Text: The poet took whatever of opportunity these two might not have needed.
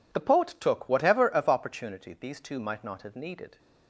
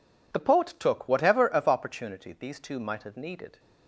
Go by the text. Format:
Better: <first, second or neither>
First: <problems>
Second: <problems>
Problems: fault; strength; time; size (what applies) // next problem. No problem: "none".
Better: first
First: none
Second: skips "not"; at 3.0 s